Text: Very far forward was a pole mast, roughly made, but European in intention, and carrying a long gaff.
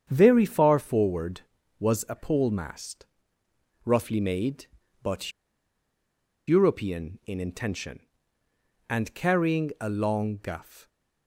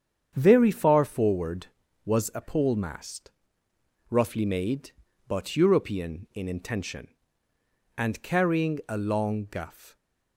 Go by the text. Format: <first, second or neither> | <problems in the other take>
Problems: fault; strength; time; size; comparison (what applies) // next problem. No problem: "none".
second | starts louder than the rest; strong; until 1.1 s; 8 dB; strong in the second // pauses between "but" and "European"; at 5.3 s; 1.1 s long